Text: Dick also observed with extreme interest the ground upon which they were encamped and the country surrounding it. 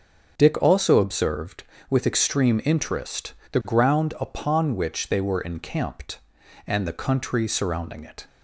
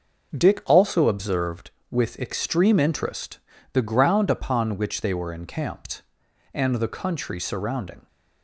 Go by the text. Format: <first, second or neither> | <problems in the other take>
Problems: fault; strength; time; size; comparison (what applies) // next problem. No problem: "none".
first | starts louder than the rest; until 1.4 s; 6 dB; also in the first // pauses between "interest" and "the"; slight; at 3.3 s; 0.34 s long; slight in the first // stops before "it"; at 8.0 s